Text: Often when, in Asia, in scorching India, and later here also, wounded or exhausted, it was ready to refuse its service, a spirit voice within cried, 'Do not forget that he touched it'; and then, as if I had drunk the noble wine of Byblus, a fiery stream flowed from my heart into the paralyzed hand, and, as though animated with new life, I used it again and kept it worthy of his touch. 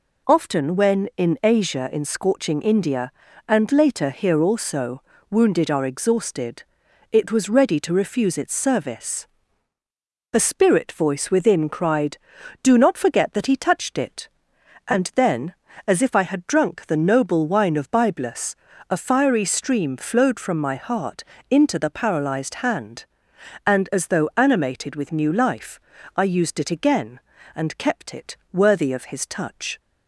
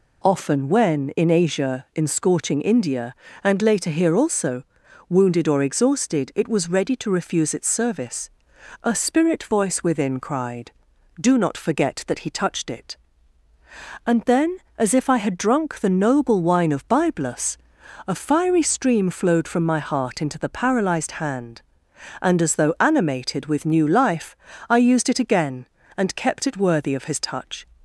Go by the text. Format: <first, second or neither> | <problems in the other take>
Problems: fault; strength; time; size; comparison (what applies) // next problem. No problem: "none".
second | says "are" for "or"; at 5.6 s // pauses between "heart" and "into"; slight; at 21.2 s; 0.26 s long // pauses between "it" and "worthy"; slight; at 28.3 s; 0.16 s long